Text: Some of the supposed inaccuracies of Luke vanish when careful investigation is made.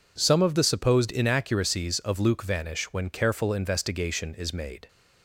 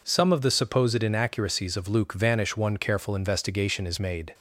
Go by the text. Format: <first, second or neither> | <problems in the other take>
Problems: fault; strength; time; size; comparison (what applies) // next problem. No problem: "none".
first | says "one" for "when"; at 2.5 s